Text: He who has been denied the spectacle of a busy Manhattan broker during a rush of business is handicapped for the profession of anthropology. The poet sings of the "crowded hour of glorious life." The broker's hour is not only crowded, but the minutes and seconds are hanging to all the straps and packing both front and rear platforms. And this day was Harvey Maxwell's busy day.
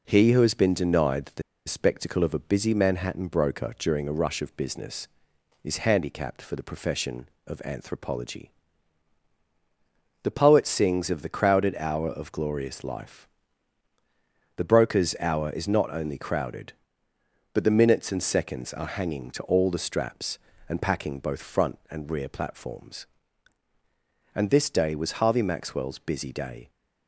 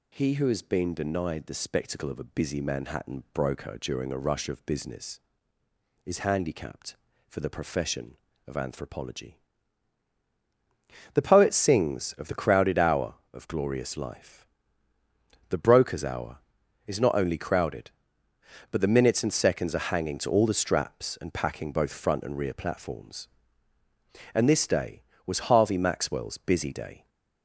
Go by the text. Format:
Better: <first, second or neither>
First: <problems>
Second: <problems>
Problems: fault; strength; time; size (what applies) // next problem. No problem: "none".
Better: second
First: pauses between "the" and "spectacle"; slight; at 1.4 s; 0.25 s long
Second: none